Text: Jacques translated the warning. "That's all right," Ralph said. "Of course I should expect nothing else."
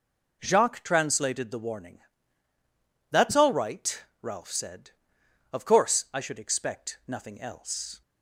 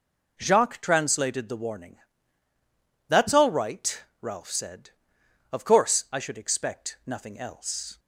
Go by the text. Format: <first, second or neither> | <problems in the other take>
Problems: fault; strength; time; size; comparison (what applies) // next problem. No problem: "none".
neither | none